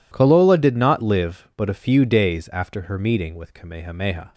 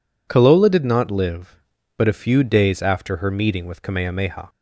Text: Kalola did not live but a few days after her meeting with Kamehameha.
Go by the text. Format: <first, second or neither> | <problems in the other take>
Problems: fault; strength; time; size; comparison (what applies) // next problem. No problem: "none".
neither | none